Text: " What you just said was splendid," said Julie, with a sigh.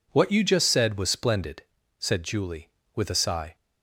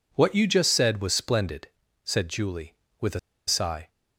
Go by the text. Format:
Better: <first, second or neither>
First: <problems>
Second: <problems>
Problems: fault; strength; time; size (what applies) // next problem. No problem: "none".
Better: first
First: none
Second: pauses between "a" and "sigh"; slight; at 3.1 s; 0.28 s long